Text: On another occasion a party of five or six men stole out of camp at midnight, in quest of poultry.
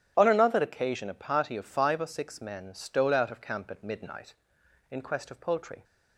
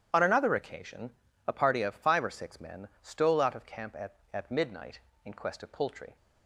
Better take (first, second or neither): first